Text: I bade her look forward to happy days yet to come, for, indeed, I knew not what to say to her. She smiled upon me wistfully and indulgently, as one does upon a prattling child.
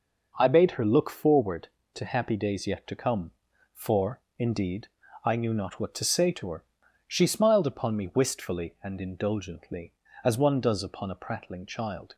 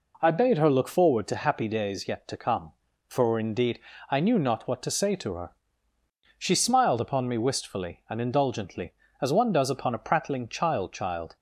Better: first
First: none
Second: says "child" twice; at 10.9 s

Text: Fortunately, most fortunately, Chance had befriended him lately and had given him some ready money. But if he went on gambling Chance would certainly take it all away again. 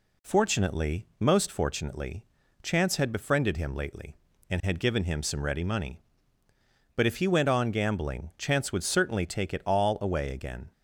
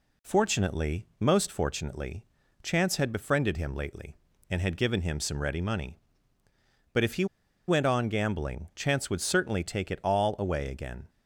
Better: first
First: none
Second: pauses between "he" and "went"; at 7.2 s; 0.42 s long

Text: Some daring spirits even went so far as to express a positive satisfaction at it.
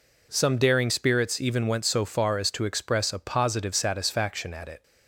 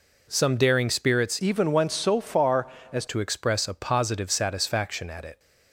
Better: first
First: none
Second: changes voice from "even" to "as"; from 1.3 to 3.0 s; 1.7 s long

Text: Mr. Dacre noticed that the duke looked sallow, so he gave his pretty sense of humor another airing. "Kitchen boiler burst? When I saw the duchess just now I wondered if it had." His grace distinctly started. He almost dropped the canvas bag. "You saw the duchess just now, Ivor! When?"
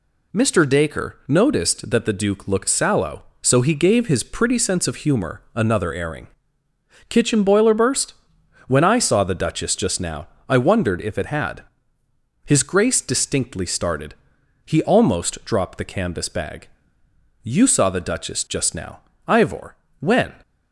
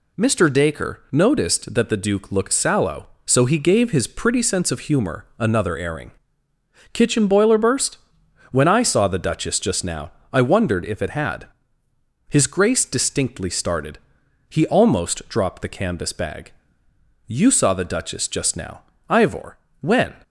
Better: neither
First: pauses between "now" and "I"; slight; at 10.2 s; 0.22 s long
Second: pauses between "now" and "I"; slight; at 10.1 s; 0.22 s long

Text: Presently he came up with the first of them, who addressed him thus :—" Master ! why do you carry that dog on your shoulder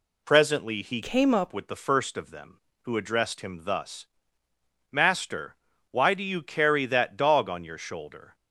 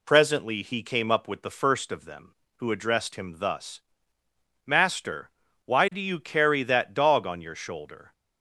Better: second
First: changes voice from "came" to "up"; from 1.0 to 1.5 s; 0.5 s long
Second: none

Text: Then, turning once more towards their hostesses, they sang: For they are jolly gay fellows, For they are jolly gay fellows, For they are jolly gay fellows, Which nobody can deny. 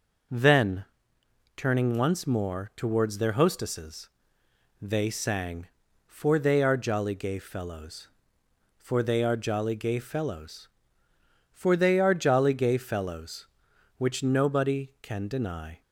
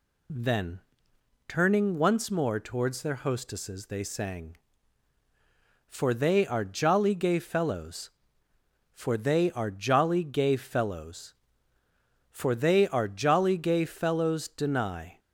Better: first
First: none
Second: skips "Which nobody can"; at 14.4 s

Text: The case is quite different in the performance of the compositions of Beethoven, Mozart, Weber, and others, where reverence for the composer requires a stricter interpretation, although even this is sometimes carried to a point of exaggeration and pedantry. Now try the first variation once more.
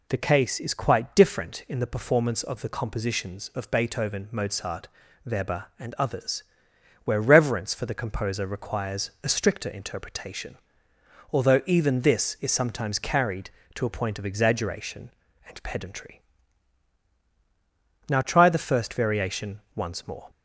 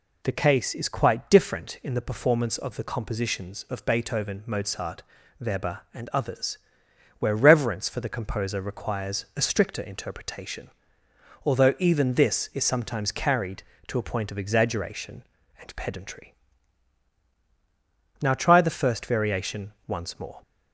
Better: neither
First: pauses between "variation" and "once"; slight; at 19.5 s; 0.16 s long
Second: pauses between "variation" and "once"; slight; at 19.7 s; 0.16 s long

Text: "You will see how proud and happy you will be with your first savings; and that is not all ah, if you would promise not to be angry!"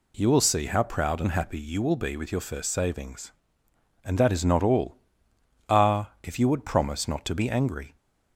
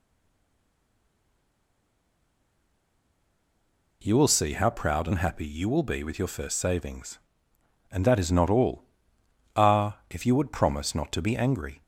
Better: first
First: pauses between "all" and "ah"; noticeable; at 4.9 s; 0.72 s long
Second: stays silent before the first word; strong; until 4.0 s; 4.0 s long // pauses between "all" and "ah"; noticeable; at 8.8 s; 0.72 s long

